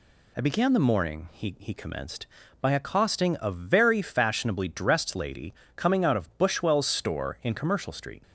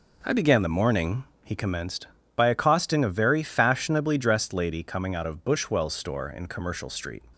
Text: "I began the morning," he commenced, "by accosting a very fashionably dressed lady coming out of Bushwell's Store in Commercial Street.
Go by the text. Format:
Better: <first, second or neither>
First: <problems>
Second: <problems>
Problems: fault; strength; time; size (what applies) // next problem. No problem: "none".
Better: second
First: says "he" twice; at 1.5 s // pauses between "lady" and "coming"; slight; at 5.5 s; 0.24 s long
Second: none